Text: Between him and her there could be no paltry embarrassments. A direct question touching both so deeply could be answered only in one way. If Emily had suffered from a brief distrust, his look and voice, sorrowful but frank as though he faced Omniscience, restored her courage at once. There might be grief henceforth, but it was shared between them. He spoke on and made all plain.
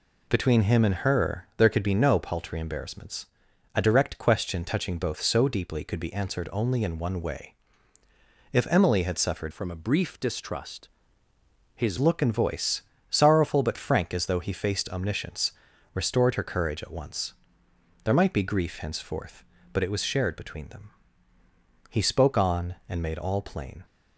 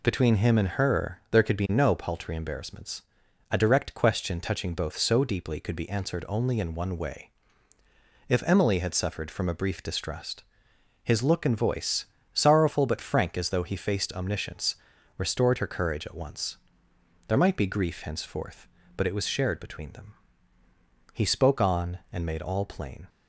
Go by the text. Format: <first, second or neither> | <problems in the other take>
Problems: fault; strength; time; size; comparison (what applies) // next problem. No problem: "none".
second | changes voice from "from" to "his"; from 9.5 to 11.9 s; 2.4 s long